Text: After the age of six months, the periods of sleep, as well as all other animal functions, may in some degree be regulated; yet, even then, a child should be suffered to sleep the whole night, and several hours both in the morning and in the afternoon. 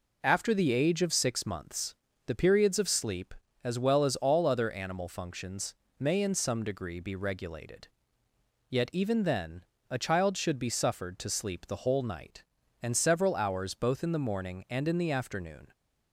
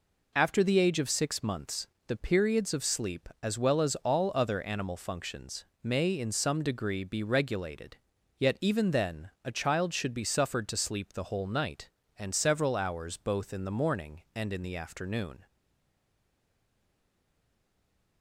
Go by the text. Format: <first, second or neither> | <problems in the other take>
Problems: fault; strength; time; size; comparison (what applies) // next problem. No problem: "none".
first | stays silent after the last word; strong; from 15.4 s on; 2.8 s long